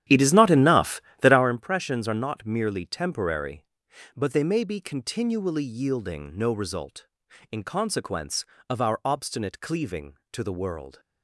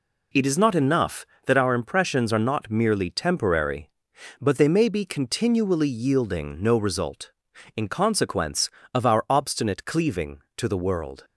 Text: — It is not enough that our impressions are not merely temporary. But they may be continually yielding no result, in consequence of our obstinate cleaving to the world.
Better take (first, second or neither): second